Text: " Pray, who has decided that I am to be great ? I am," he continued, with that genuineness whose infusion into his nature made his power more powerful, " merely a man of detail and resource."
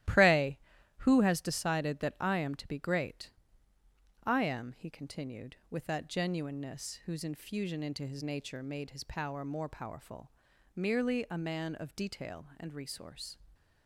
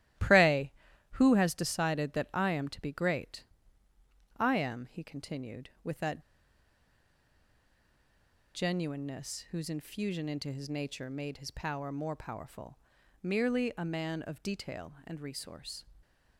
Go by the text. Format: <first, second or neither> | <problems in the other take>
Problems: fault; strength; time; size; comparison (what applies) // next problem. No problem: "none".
first | starts louder than the rest; strong; until 1.5 s; 14 dB; strong in the first // pauses between "that" and "genuineness"; strong; at 6.2 s; 2.3 s long